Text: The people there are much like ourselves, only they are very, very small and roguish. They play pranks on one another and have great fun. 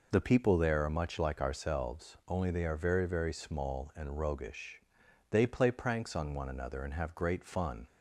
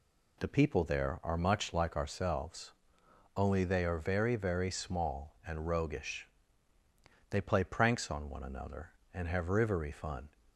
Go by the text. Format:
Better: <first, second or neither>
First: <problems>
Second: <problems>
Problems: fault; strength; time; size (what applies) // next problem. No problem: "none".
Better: first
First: none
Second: says "rivery" for "great"; at 9.4 s